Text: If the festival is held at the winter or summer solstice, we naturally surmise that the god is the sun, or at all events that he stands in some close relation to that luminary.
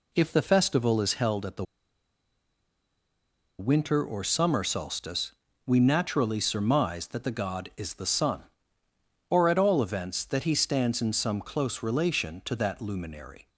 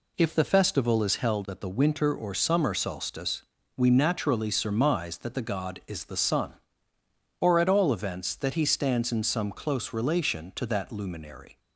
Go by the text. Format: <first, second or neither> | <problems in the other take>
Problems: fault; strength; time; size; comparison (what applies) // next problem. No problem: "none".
second | pauses between "the" and "winter"; strong; at 1.6 s; 1.9 s long